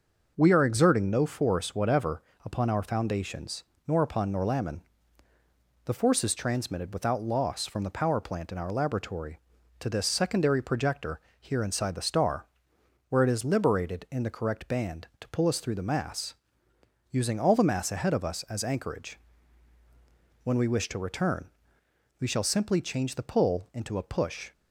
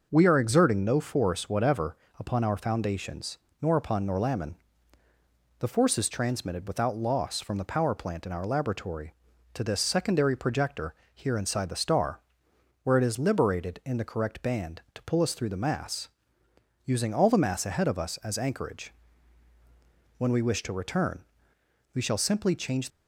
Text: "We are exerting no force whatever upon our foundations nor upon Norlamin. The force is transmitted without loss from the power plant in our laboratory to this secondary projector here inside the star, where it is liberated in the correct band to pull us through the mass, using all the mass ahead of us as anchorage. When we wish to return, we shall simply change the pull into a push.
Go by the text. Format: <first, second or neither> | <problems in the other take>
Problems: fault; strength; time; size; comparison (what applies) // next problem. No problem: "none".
first | pauses between "whatever" and "upon"; slight; at 1.9 s; 0.22 s long; slight in the first // pauses between "foundations" and "nor"; slight; at 3.3 s; 0.24 s long; slight in the first // pauses between "projector" and "here"; slight; at 10.9 s; 0.20 s long; slight in the first // stops before "the pull into a push"; at 22.8 s